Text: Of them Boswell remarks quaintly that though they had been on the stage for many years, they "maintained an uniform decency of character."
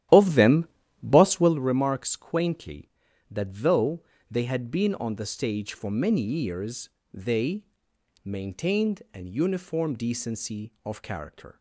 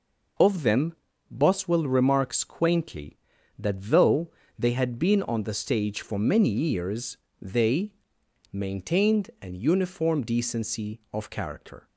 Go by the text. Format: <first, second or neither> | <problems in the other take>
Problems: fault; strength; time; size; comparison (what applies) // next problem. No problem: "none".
second | starts louder than the rest; strong; until 1.6 s; 12.5 dB // pauses between "them" and "Boswell"; slight; at 0.6 s; 0.36 s long; slight in the second // pauses between "though" and "they"; slight; at 4.0 s; 0.28 s long; slight in the second // pauses between "they" and "maintained"; noticeable; at 7.6 s; 0.58 s long; noticeable in the second